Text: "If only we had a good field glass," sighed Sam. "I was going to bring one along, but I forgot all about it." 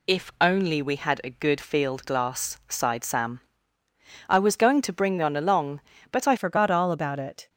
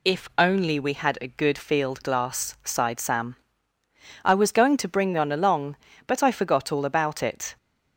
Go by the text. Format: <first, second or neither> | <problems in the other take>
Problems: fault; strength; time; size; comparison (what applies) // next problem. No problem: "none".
second | changes voice at "forgot"; from 6.3 s on; 1.1 s long